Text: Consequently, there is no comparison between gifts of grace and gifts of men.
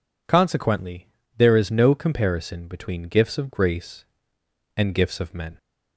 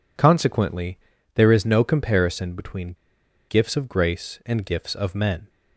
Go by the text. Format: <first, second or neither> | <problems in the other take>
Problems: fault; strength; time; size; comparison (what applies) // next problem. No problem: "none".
first | pauses between "between" and "gifts"; noticeable; at 2.9 s; 0.53 s long